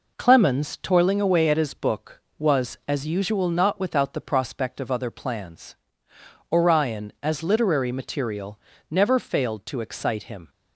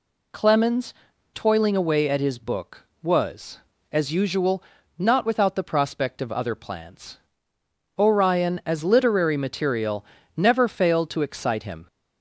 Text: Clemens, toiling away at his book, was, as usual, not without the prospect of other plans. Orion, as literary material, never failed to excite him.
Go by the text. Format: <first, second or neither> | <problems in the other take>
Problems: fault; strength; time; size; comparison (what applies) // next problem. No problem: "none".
neither | none